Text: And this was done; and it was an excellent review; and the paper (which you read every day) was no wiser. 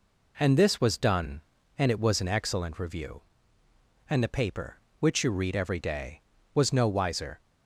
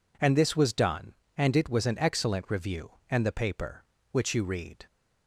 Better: first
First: none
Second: stops before "every day was no wiser"; at 4.8 s

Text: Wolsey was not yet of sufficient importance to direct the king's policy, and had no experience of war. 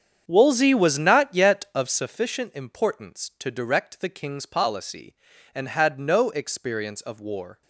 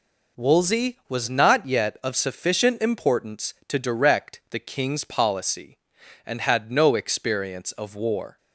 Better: second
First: starts louder than the rest; strong; until 2.1 s; 8 dB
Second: none

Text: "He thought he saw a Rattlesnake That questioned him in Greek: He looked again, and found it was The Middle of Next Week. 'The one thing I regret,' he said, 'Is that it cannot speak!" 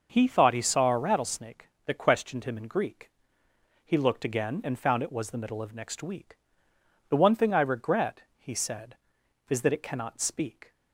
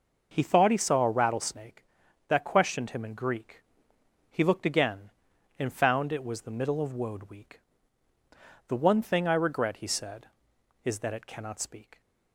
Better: first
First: none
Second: says "Woad" for "Next"; at 6.9 s

